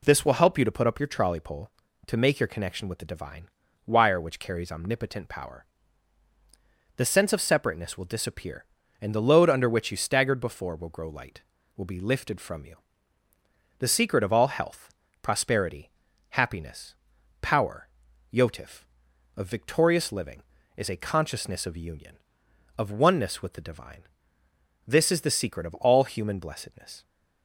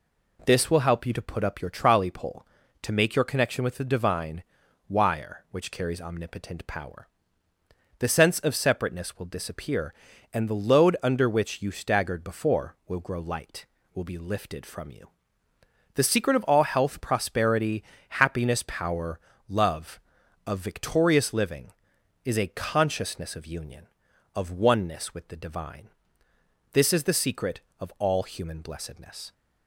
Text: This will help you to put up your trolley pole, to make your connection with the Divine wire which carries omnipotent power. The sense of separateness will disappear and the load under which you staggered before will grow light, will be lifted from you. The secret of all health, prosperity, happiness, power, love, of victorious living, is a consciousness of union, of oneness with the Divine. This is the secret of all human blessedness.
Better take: second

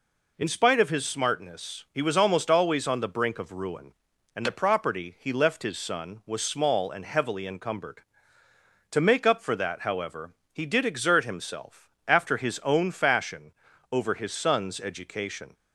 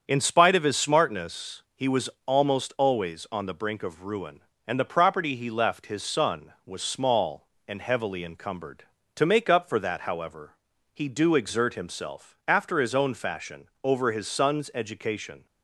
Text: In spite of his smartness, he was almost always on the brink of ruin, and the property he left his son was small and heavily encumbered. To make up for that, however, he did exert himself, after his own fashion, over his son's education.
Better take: first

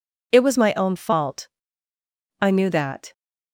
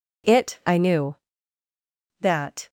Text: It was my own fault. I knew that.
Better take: first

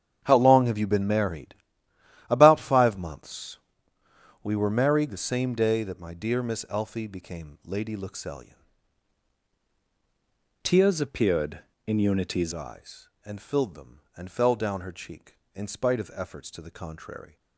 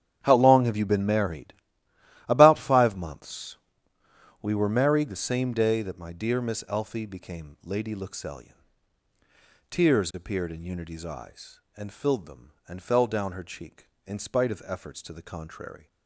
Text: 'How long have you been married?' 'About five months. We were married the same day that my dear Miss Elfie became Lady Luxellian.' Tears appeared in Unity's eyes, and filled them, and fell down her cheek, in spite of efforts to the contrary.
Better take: second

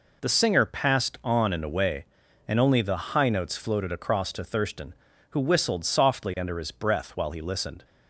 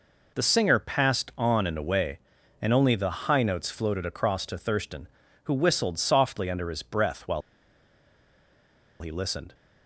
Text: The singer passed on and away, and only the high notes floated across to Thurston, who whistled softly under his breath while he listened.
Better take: first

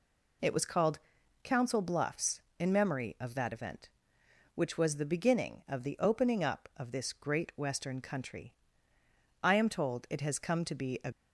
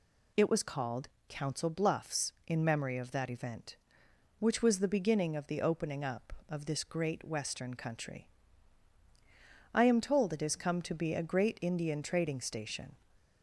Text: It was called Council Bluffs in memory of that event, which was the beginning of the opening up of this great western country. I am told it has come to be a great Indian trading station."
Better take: second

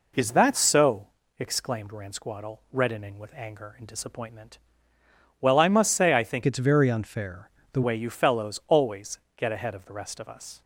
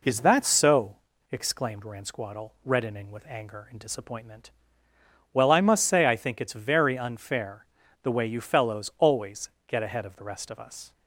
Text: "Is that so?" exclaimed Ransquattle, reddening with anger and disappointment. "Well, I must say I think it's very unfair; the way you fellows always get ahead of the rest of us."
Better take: second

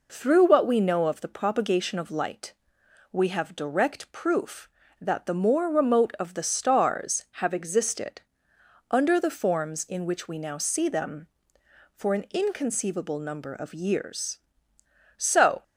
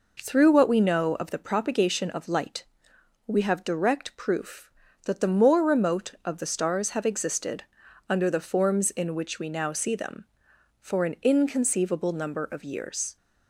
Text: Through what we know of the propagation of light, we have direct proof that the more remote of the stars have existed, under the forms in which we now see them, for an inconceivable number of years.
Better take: second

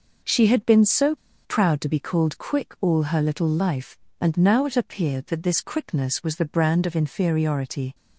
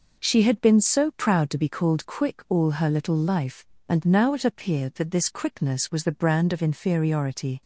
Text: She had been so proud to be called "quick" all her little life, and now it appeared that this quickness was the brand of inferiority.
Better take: second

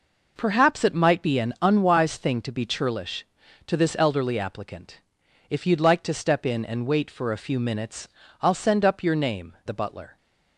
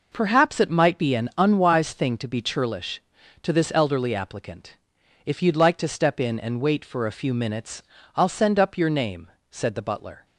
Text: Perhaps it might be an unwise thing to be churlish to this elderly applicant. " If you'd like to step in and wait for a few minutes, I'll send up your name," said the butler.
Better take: second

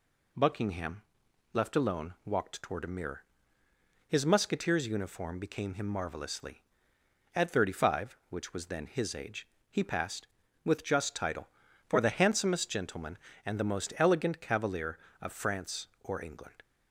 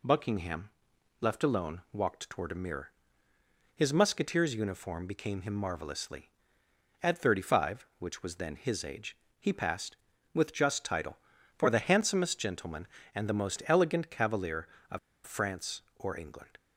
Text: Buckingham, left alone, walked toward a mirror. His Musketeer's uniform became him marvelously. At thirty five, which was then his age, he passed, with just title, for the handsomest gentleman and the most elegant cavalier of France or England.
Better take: first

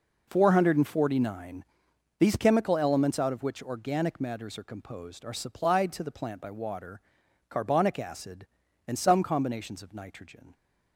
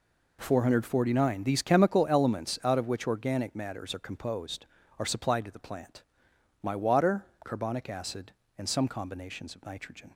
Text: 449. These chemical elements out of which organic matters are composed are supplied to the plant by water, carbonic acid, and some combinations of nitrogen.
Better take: first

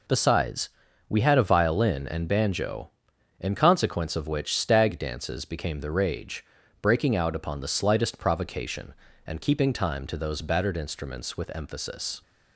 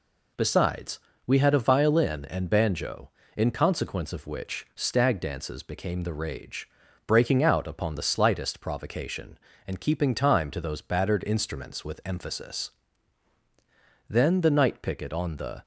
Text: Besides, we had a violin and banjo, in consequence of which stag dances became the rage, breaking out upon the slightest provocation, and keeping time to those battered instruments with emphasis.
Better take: first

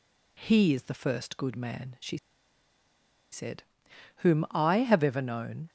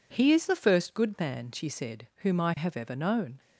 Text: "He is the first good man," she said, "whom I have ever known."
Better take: second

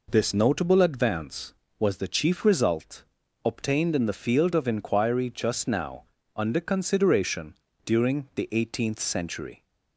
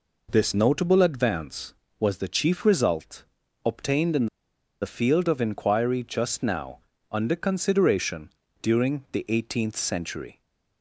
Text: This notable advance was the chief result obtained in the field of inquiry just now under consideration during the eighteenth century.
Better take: first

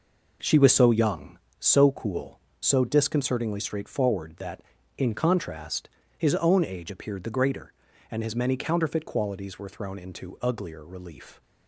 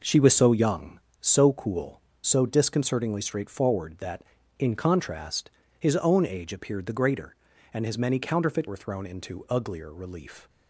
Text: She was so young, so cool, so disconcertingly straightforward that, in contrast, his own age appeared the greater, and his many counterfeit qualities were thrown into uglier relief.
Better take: first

